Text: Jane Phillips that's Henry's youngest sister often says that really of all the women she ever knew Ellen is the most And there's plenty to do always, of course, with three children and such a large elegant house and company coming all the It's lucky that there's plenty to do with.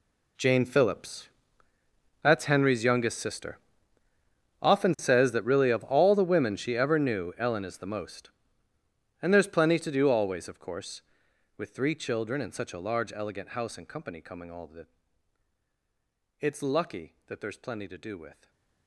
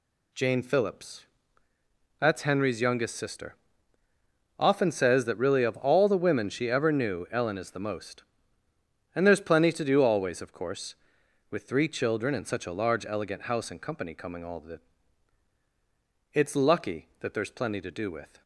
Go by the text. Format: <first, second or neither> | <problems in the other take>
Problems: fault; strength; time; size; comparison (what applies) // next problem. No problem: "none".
second | gets quieter; strong; throughout; 17.5 dB // pauses between "Phillips" and "that's"; noticeable; at 1.2 s; 0.94 s long; noticeable in the second // pauses between "sister" and "often"; at 3.5 s; 1.0 s long; also in the second // pauses between "the" and "It's"; strong; at 14.8 s; 1.5 s long; strong in the second // stays silent after the last word; slight; from 18.3 s on; 0.5 s long